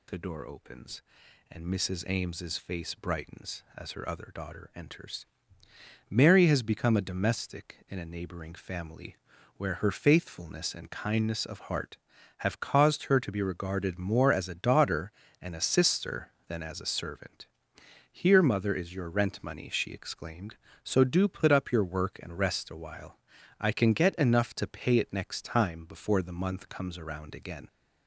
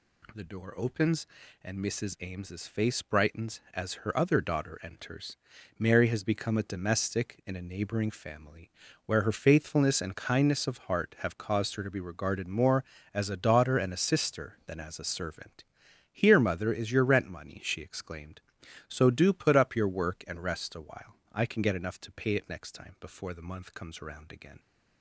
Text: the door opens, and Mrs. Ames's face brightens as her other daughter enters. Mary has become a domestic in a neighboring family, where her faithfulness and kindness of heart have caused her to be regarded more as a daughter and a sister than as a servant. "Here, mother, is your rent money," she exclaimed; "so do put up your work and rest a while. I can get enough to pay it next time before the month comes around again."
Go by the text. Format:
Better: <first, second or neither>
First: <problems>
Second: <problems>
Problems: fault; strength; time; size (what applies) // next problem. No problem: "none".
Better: neither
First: none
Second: none